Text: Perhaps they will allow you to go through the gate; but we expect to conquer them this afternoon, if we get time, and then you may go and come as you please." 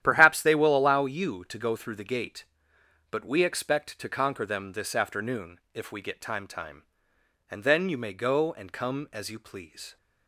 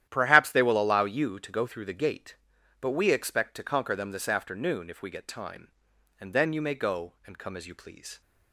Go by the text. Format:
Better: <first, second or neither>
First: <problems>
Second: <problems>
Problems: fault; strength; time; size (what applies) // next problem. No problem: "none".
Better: second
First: starts louder than the rest; strong; until 1.0 s; 11 dB // says "time" twice; at 6.4 s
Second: starts louder than the rest; strong; until 1.1 s; 11 dB